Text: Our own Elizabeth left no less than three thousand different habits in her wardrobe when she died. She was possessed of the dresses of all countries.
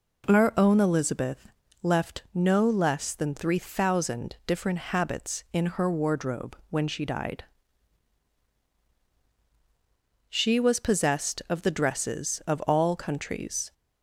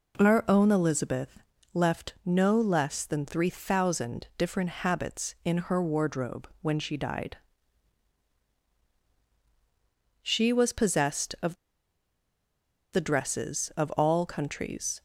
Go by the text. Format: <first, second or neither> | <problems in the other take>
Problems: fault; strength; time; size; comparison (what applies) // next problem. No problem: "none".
first | pauses between "Elizabeth" and "left"; slight; at 1.4 s; 0.32 s long; slight in the first // pauses between "of" and "the"; strong; at 11.5 s; 1.3 s long